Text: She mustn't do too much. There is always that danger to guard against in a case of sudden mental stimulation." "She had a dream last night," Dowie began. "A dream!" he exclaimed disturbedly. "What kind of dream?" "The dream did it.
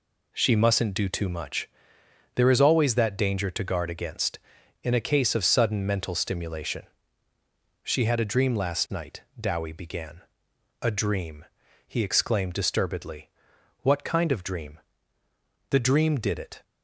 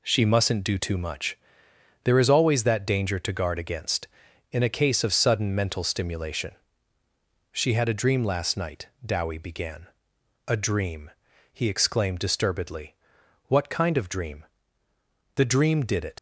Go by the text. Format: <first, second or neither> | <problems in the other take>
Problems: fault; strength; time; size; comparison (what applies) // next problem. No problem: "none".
first | leaves "it" unfinished; at 16.1 s; 95 ms